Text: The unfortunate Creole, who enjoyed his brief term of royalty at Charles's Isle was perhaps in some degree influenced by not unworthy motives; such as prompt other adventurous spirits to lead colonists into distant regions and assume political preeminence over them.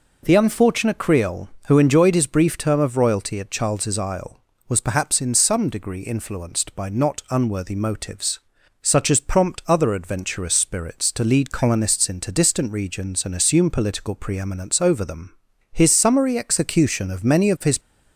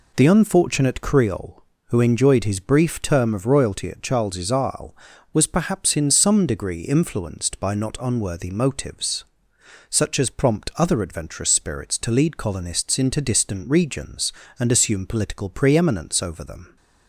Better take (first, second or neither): second